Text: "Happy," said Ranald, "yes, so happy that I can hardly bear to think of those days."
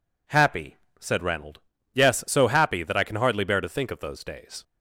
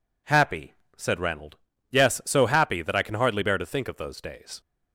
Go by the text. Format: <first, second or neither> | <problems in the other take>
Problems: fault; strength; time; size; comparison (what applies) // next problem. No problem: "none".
neither | none